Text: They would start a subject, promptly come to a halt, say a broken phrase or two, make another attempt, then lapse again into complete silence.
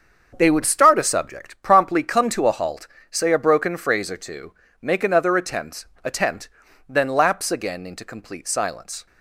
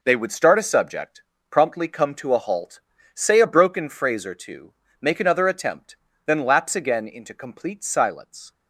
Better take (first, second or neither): second